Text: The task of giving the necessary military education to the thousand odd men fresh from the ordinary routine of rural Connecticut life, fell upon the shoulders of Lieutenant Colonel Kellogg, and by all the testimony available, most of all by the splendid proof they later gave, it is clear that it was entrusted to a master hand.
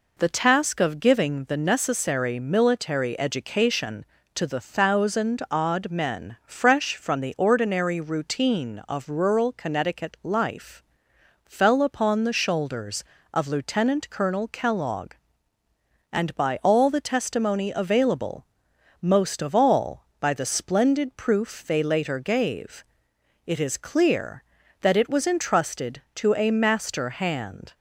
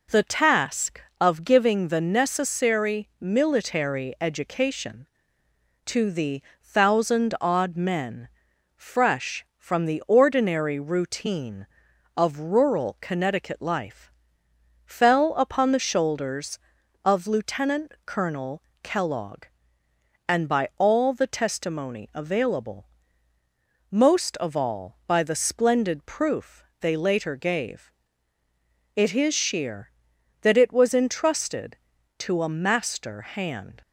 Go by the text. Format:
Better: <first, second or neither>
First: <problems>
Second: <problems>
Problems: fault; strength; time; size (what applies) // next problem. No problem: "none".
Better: first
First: none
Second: pauses between "the" and "thousand"; slight; at 6.4 s; 0.22 s long // pauses between "men" and "fresh"; noticeable; at 8.2 s; 0.48 s long // pauses between "Colonel" and "Kellogg"; slight; at 18.6 s; 0.18 s long // pauses between "proof" and "they"; slight; at 26.6 s; 0.18 s long // says "sheer" for "clear"; at 29.3 s